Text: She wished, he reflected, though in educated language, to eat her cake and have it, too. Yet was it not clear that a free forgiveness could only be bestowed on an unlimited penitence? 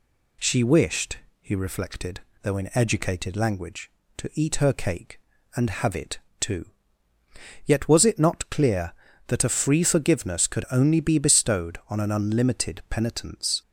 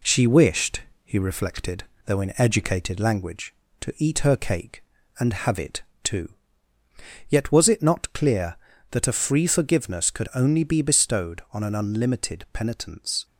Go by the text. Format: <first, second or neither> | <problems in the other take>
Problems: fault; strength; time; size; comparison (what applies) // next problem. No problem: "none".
first | gets quieter; slight; throughout; 2 dB